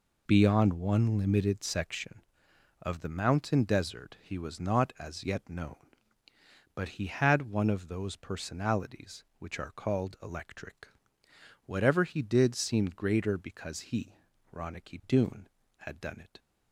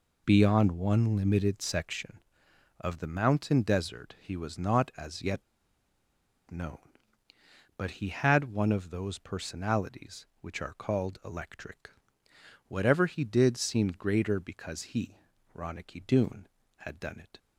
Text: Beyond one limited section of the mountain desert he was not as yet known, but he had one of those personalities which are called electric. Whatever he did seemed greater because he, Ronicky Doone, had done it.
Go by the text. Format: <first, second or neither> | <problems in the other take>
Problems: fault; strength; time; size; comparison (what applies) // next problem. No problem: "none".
first | pauses between "yet" and "known"; at 5.4 s; 1.0 s long